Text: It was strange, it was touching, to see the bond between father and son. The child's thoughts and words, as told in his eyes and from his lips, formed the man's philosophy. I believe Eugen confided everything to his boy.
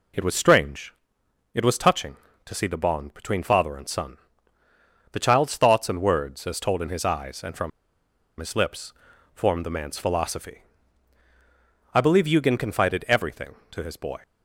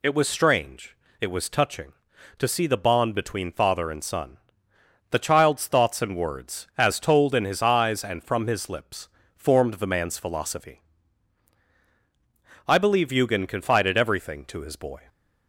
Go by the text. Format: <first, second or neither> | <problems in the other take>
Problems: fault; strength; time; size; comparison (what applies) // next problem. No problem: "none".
second | pauses between "from" and "his"; noticeable; at 7.7 s; 0.70 s long